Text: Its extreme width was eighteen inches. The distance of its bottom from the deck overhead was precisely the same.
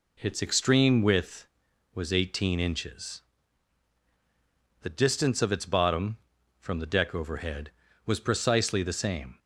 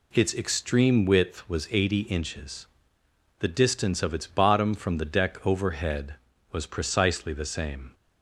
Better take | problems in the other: first | says "eighty" for "eighteen"; at 1.7 s

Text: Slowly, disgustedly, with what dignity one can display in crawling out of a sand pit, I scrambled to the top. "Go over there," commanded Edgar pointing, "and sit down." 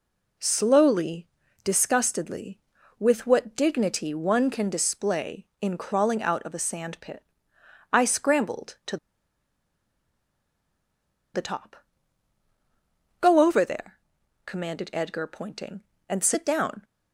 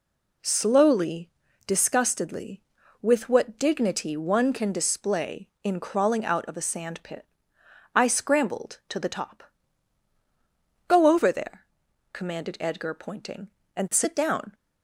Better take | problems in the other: second | pauses between "to" and "the"; strong; at 8.9 s; 2.3 s long

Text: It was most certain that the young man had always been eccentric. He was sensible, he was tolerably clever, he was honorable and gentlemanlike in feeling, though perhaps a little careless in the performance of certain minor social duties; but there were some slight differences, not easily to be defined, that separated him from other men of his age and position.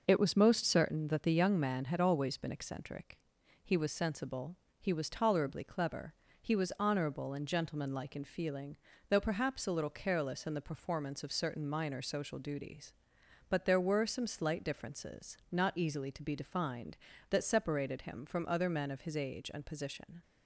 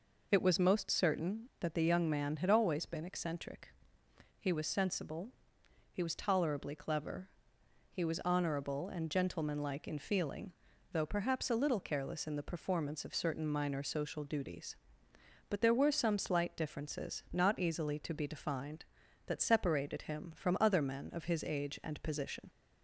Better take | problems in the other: neither | none

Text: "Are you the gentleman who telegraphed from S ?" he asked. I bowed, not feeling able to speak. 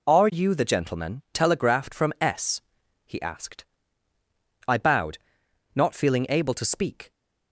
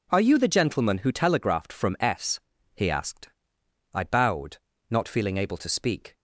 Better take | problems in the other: second | skips "who"; at 1.2 s

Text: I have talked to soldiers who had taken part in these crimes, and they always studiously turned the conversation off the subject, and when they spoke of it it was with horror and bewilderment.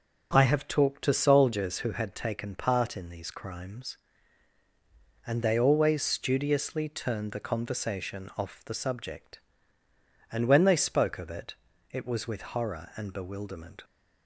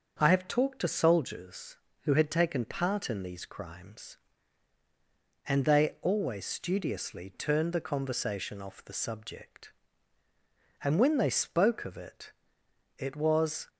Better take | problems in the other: first | starts louder than the rest; until 1.2 s; 6.5 dB // pauses between "it" and "it"; noticeable; at 12.3 s; 0.66 s long; slight in the first // stops before "with horror and bewilderment"; at 13.6 s

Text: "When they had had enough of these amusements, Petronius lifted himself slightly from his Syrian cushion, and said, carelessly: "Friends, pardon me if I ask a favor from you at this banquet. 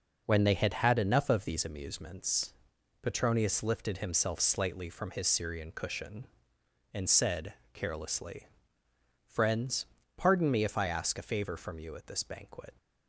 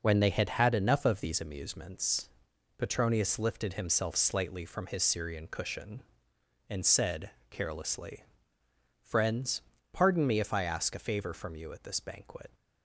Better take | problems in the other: neither | none

